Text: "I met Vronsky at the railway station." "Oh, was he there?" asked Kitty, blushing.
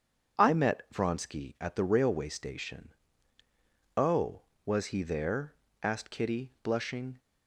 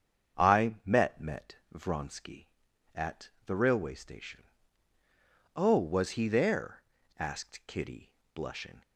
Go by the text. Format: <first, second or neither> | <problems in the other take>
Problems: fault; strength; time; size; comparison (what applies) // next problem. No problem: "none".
first | starts louder than the rest; strong; until 1.4 s; 7.5 dB; strong in the first // says "met" twice; at 1.1 s // pauses between "at" and "the"; slight; at 3.2 s; 0.16 s long